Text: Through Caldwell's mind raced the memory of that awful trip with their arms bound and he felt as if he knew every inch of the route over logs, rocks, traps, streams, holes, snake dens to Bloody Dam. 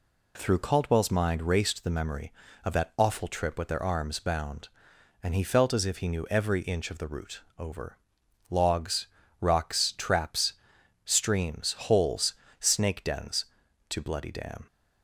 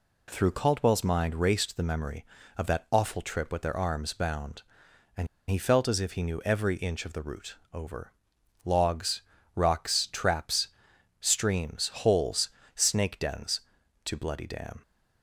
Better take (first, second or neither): first